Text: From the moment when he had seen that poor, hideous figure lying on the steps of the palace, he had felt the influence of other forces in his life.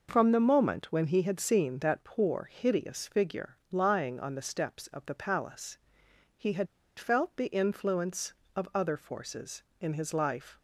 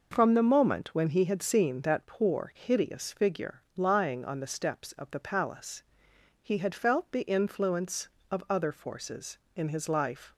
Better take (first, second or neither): second